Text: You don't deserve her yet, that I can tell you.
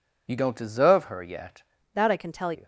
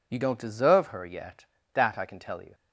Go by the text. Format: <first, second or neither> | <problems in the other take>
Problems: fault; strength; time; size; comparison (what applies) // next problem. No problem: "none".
second | changes voice from "that" to "tell"; from 1.9 to 2.5 s; 0.6 s long